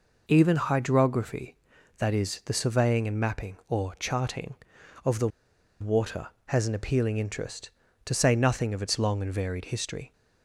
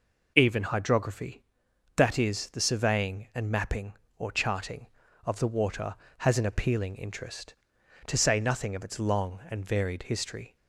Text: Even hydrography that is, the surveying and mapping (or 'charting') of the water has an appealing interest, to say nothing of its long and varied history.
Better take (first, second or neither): second